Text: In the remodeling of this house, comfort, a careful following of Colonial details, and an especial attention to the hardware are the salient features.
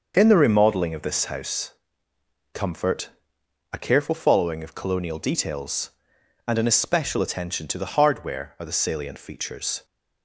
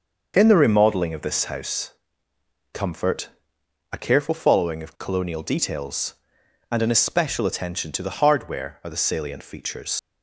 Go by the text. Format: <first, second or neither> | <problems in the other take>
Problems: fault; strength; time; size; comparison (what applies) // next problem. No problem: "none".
first | starts louder than the rest; until 1.3 s; 6 dB; also in the first // leaves "features" unfinished; at 9.9 s; 100 ms